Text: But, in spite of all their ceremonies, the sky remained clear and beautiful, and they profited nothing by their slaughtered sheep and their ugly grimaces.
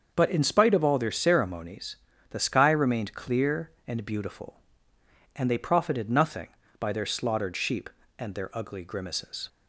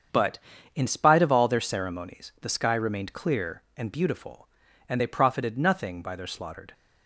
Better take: first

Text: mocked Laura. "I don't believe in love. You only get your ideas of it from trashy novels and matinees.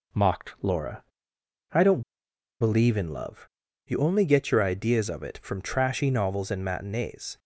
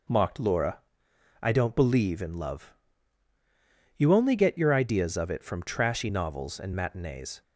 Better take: second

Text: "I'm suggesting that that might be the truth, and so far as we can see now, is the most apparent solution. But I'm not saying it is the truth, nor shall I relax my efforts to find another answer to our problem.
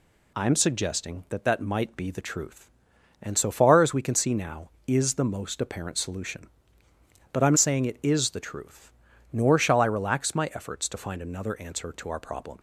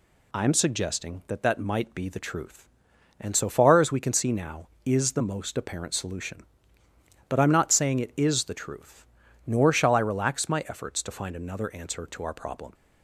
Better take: second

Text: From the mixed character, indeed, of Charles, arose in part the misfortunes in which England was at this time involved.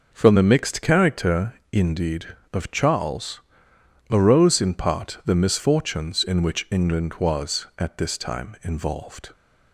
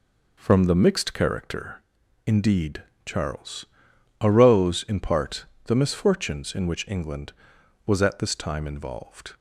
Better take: first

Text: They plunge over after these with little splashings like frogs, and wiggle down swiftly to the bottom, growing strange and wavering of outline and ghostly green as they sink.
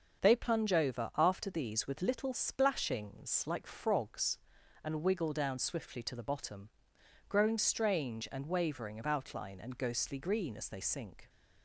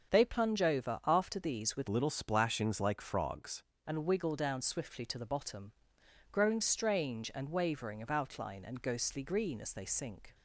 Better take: first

